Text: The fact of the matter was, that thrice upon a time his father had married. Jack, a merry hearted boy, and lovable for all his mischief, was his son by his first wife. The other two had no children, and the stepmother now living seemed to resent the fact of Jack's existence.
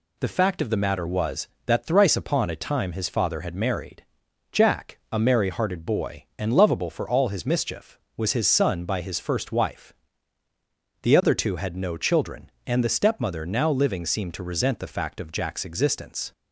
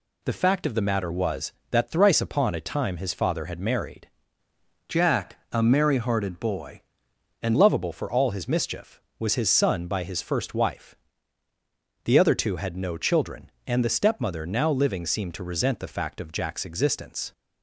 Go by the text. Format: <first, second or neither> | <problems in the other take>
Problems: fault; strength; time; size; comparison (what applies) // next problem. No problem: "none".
first | changes voice from "Jack" to "and"; from 4.8 to 7.5 s; 2.7 s long